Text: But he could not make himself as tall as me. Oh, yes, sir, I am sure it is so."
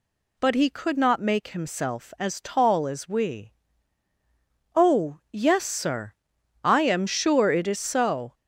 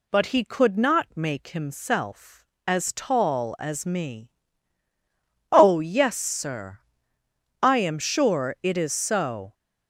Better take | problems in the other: second | says "we" for "me"; at 3.0 s

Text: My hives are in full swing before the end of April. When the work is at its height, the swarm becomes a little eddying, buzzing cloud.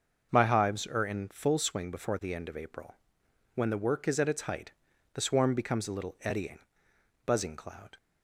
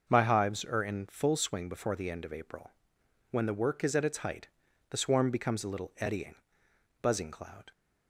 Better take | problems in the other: neither | starts louder than the rest; noticeable; the same in both

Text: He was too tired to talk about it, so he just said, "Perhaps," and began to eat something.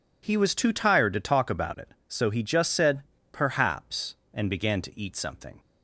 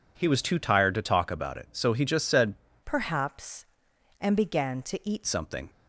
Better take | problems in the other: first | changes voice from "Perhaps" to "eat"; from 2.8 to 5.2 s; 2.4 s long

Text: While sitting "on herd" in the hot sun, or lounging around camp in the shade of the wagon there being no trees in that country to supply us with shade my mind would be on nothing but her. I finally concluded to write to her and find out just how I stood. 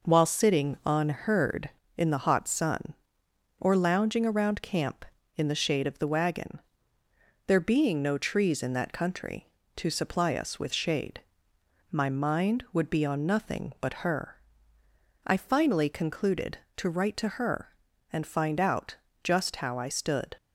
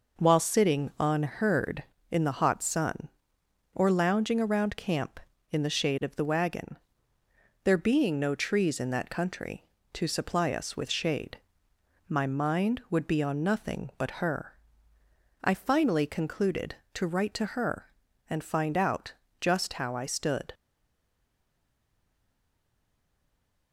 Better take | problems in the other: first | pauses between "wagon" and "there"; noticeable; at 6.7 s; 0.88 s long; noticeable in the first // pauses between "shade" and "my"; noticeable; at 11.3 s; 0.70 s long; noticeable in the first // pauses between "out" and "just"; slight; at 19.1 s; 0.26 s long; slight in the first // stays silent after the last word; strong; from 20.5 s on; 3.2 s long

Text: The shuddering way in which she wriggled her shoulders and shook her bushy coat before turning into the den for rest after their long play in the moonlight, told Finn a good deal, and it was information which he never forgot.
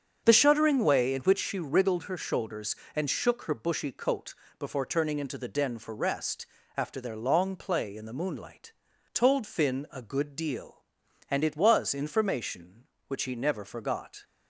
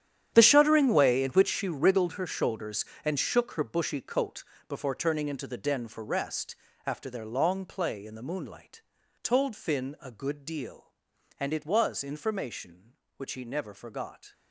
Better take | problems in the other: first | gets quieter; strong; throughout; 15.5 dB // starts louder than the rest; strong; until 1.3 s; 9.5 dB; also in the first // pauses between "coat" and "before"; slight; at 4.4 s; 0.24 s long; slight in the first // pauses between "rest" and "after"; slight; at 6.5 s; 0.32 s long; slight in the first

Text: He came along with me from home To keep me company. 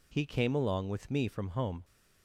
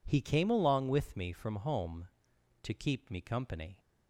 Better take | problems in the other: second | stops before "To keep me company"; at 1.8 s

